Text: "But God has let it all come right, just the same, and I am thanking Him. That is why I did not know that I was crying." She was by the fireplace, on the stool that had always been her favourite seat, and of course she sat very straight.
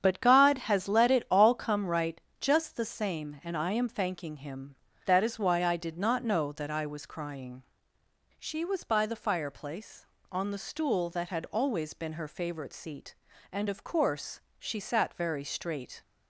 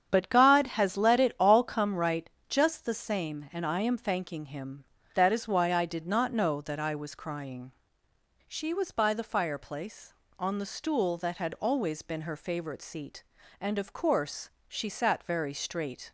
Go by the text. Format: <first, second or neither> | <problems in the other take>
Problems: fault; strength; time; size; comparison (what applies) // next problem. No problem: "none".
neither | starts louder than the rest; strong; the same in both // pauses between "course" and "she"; slight; the same in both